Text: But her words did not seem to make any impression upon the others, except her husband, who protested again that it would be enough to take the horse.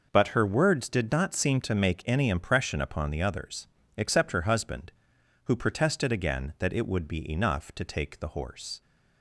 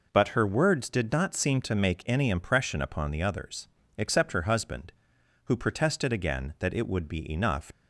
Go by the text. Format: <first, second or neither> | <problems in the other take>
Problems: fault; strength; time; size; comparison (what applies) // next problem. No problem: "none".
first | stops before "to take the horse"; at 7.7 s